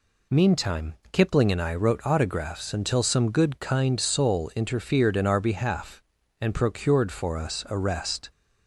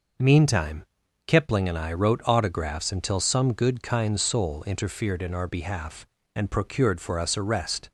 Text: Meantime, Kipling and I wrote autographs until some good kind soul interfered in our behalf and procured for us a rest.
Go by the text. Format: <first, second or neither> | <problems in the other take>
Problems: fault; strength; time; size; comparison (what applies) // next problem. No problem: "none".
neither | none